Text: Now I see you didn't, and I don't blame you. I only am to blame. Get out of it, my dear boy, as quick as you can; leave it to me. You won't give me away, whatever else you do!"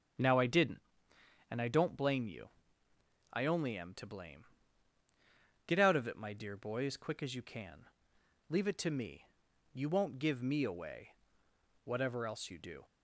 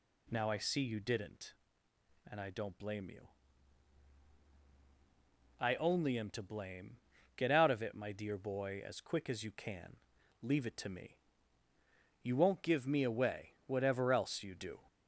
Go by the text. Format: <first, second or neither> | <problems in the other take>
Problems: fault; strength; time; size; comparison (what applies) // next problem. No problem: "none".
second | starts louder than the rest; strong; until 1.8 s; 8.5 dB // skips "see you"; at 0.4 s